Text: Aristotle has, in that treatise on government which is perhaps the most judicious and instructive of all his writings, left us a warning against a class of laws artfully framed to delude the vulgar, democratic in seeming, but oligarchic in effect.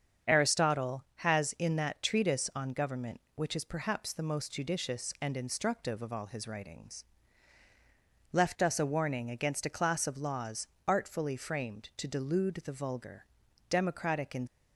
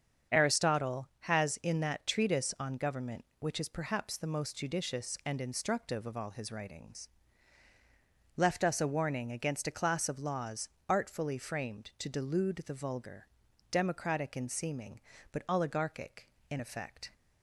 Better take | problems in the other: second | starts louder than the rest; strong; until 1.4 s; 7.5 dB; strong in the second // pauses between "laws" and "artfully"; slight; at 10.6 s; 0.20 s long; slight in the second // stops before "seeming but oligarchic in effect"; at 14.4 s

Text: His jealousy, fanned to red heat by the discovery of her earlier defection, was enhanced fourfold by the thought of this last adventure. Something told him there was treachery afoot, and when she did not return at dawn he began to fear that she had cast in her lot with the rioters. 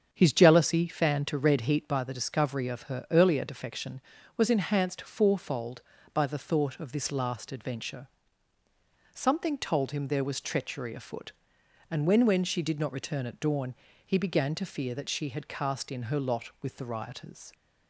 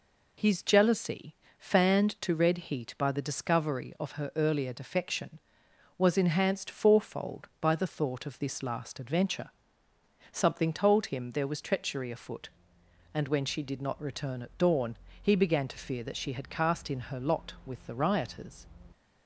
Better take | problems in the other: second | starts louder than the rest; strong; until 1.1 s; 7 dB // says "when" twice; at 12.2 s // pauses between "dawn" and "he"; slight; at 13.7 s; 0.30 s long; slight in the second

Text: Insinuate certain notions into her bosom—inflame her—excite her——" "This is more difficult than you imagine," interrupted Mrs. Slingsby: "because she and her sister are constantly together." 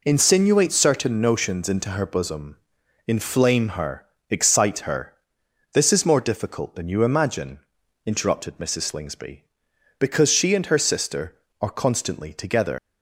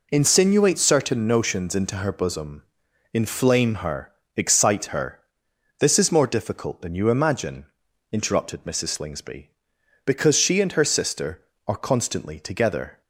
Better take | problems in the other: second | leaves "together" unfinished; at 12.7 s; 160 ms

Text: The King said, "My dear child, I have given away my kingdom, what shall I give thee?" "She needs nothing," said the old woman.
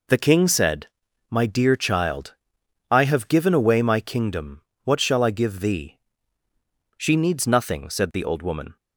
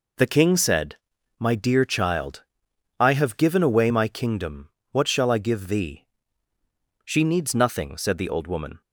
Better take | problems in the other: neither | none

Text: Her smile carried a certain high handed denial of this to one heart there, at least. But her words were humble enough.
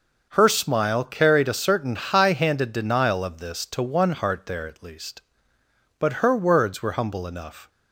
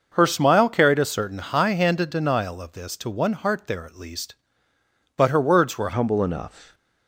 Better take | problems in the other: first | changes voice at "humble"; from 5.9 s on; 0.8 s long

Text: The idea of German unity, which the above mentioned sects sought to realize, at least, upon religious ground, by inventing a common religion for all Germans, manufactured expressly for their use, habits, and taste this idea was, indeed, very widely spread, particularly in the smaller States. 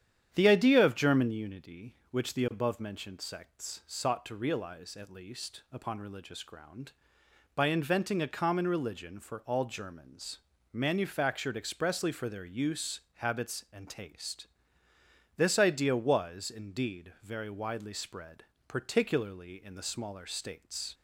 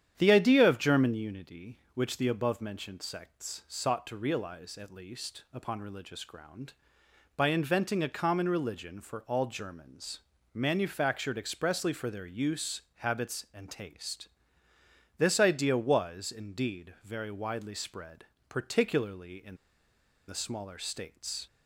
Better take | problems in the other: first | starts louder than the rest; strong; until 1.1 s; 9.5 dB; strong in the first // pauses between "taste" and "this"; noticeable; at 14.2 s; 0.90 s long; noticeable in the first // pauses between "in" and "the"; noticeable; at 19.5 s; 0.72 s long

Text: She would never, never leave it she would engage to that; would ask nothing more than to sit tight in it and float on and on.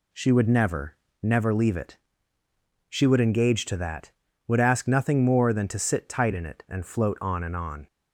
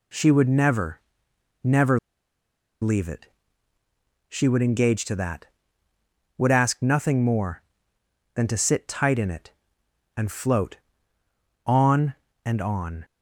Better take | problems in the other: first | pauses between "never" and "leave"; noticeable; at 1.9 s; 0.83 s long // pauses between "it" and "she"; at 3.2 s; 1.0 s long; noticeable in the first

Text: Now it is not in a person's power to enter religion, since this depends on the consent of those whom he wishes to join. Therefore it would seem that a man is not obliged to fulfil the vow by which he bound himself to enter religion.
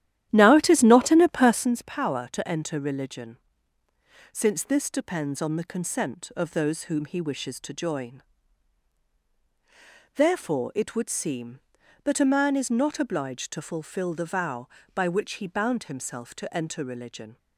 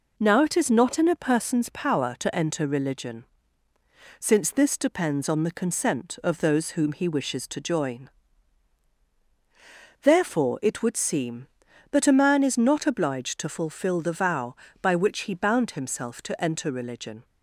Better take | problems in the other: second | starts louder than the rest; strong; until 1.8 s; 12 dB

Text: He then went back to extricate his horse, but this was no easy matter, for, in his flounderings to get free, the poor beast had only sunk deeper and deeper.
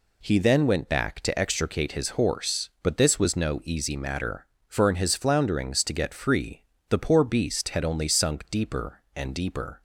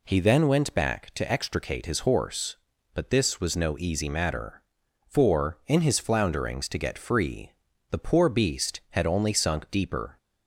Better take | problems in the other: first | stops before "and deeper"; at 10.1 s

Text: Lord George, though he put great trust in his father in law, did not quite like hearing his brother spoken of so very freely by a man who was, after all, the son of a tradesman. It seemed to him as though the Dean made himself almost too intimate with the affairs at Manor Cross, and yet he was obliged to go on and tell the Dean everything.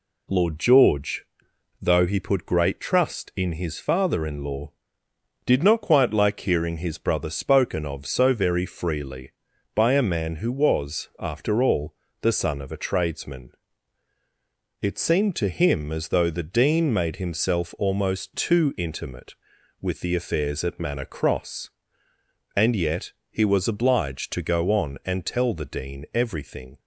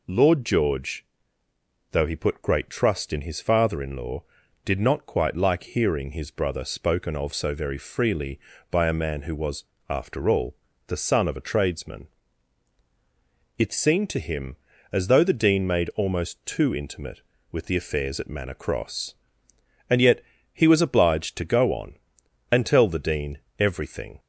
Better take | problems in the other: first | skips "himself"; at 15.9 s // pauses between "yet" and "he"; slight; at 20.2 s; 0.30 s long; slight in the first // pauses between "Dean" and "everything"; slight; at 23.3 s; 0.20 s long

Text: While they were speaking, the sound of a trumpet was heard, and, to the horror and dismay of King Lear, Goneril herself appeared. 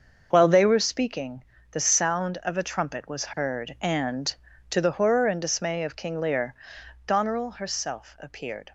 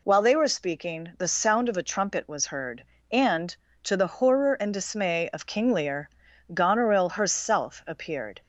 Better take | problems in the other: second | gets quieter; strong; throughout; 9.5 dB

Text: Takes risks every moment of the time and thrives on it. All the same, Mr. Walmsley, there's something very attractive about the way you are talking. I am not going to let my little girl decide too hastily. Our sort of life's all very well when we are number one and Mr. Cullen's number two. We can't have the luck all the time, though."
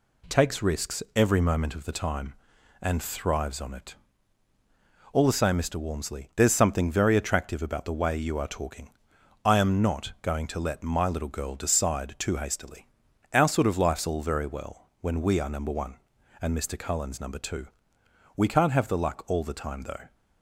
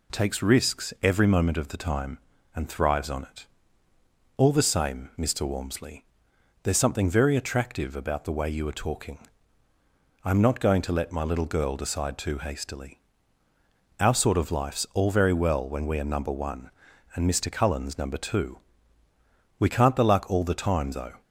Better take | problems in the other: first | skips "have"; at 19.9 s

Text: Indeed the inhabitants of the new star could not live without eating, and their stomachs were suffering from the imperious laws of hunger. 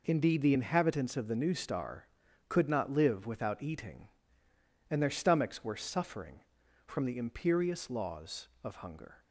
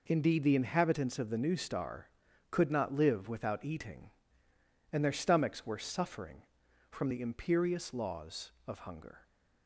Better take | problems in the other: neither | none

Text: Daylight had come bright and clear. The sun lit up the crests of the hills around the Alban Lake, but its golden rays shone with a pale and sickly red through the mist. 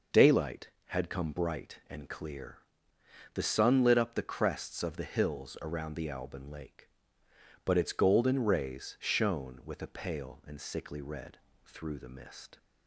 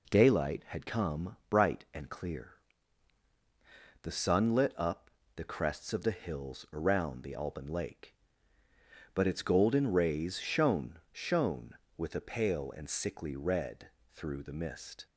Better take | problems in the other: first | pauses between "up" and "the"; slight; at 5.0 s; 0.24 s long // says "shone" twice; at 11.1 s // pauses between "red" and "through"; slight; at 13.8 s; 0.26 s long; slight in the first

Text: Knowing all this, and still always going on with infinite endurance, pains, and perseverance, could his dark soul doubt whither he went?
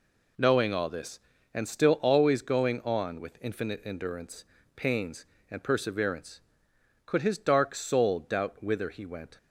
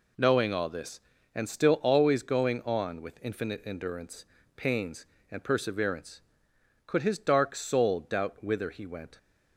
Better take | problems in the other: neither | none

